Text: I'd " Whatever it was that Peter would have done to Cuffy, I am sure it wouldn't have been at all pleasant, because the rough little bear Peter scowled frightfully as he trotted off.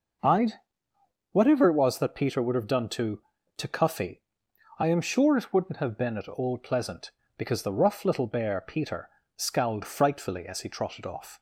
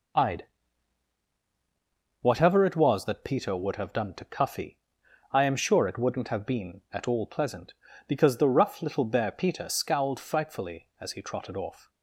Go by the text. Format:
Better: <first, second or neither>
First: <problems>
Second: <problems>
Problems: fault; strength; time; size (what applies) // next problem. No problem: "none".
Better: second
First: says "to" twice; at 3.5 s // pauses between "Peter" and "scowled"; slight; at 9.0 s; 0.28 s long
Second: none